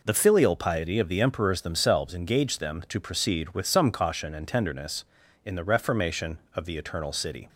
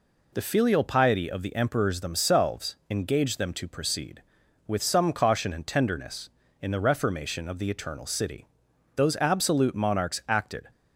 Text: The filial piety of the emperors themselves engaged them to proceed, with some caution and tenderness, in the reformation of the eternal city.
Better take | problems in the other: first | goes on to say "Those absolute monarchs acted"; strong; from 8.9 s on; 1.7 s long

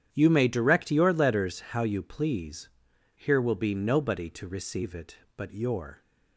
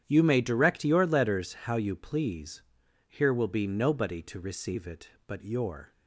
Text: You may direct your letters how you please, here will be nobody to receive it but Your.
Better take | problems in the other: neither | starts louder than the rest; strong; the same in both

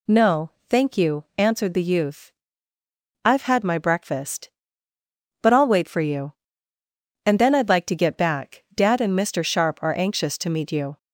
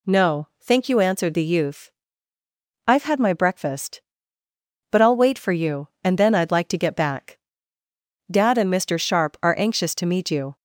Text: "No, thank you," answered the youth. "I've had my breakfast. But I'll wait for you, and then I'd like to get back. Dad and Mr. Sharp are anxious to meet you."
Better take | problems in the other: neither | none

